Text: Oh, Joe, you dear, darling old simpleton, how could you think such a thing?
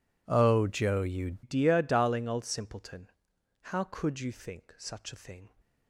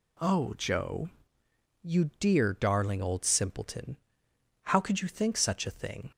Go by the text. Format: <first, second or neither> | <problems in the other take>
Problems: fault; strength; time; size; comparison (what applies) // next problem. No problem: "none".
second | changes voice at "dear"; from 1.4 s on; 4.0 s long